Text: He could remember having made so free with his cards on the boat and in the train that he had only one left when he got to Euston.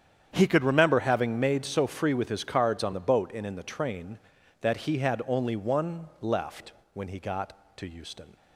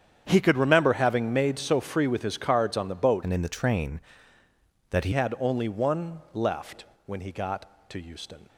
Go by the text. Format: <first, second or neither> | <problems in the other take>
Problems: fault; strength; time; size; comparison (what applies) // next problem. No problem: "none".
first | starts louder than the rest; strong; until 1.2 s; 8.5 dB; strong in the first // changes voice from "and" to "he"; from 3.2 to 5.1 s; 1.9 s long // pauses between "left" and "when"; slight; at 6.8 s; 0.22 s long; slight in the first